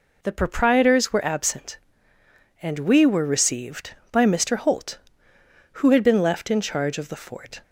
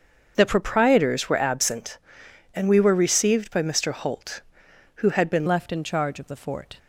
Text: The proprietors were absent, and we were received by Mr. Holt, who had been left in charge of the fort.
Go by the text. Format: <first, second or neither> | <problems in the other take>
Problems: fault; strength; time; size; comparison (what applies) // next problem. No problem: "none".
first | starts louder than the rest; until 1.3 s; 7 dB // changes voice at "left"; from 5.4 s on; 1.3 s long